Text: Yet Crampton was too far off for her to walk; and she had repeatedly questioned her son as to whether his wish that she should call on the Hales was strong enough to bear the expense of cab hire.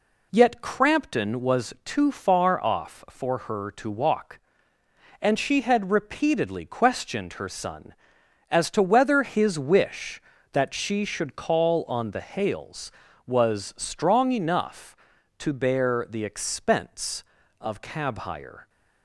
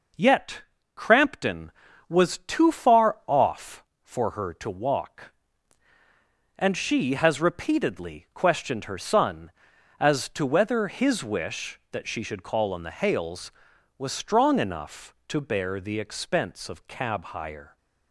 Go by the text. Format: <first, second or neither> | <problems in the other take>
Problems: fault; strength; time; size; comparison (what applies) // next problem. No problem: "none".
first | pauses between "Yet" and "Crampton"; slight; at 0.6 s; 0.32 s long // says "has" for "had"; at 7.1 s